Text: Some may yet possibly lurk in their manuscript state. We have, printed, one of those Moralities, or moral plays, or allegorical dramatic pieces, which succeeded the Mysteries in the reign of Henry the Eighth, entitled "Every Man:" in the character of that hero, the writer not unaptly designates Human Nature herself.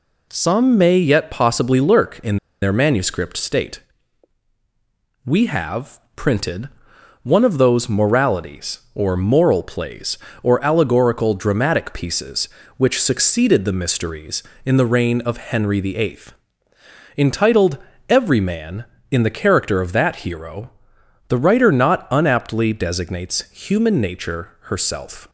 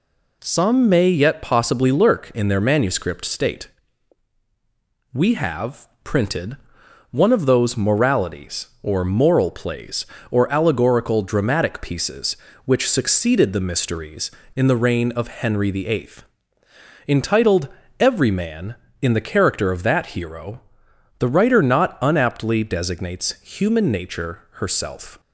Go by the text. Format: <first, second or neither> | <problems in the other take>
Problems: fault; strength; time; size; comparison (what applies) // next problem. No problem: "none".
second | pauses between "in" and "their"; slight; at 2.3 s; 0.26 s long // pauses between "entitled" and "Every"; slight; at 17.7 s; 0.32 s long; slight in the second